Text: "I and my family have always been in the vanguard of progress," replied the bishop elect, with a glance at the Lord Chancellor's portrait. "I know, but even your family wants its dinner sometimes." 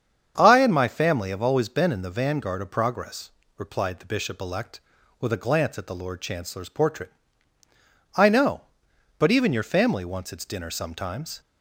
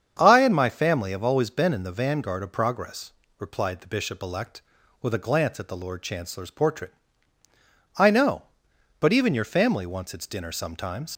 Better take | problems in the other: first | starts louder than the rest; strong; until 1.2 s; 8 dB; strong in the first // leaves "sometimes" unfinished; at 11.1 s; 60 ms

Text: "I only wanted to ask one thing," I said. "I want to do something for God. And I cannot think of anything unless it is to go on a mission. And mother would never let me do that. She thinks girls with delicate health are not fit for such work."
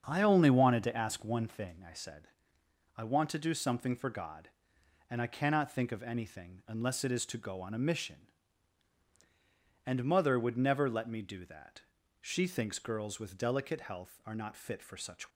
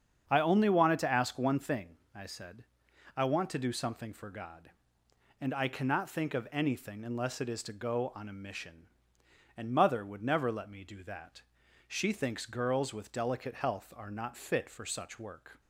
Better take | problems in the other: second | starts louder than the rest; strong; until 1.0 s; 7 dB; strong in the second // stops before "work"; at 15.3 s

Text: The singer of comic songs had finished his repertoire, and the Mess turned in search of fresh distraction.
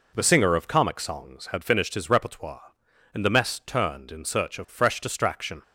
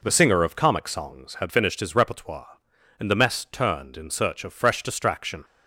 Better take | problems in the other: neither | none

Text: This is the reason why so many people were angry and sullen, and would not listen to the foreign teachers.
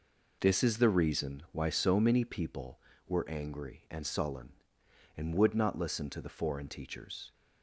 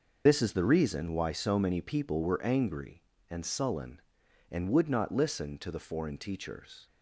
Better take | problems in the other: first | loses the start of "This"; at 0.2 s; 70 ms

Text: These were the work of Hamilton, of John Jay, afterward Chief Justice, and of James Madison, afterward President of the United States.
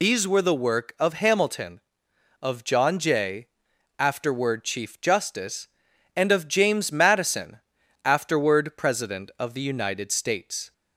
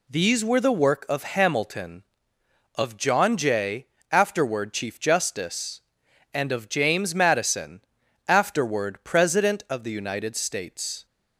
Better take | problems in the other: second | loses the start of "These"; at 0.0 s; 65 ms

